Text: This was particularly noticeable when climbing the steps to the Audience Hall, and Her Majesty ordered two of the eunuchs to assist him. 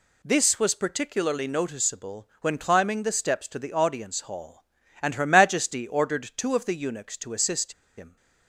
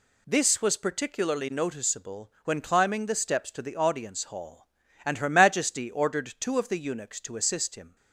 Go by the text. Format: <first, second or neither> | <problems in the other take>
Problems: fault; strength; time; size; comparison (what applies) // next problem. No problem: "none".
second | pauses between "assist" and "him"; slight; at 7.7 s; 0.25 s long